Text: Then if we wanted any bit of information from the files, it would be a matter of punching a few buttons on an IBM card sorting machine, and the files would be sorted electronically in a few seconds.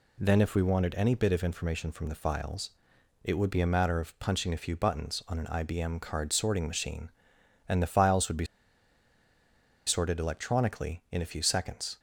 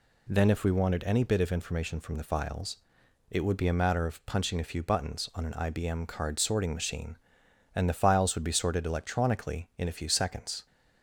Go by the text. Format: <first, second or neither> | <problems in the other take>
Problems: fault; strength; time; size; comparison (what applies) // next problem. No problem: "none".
second | pauses between "be" and "sorted"; strong; at 8.4 s; 1.4 s long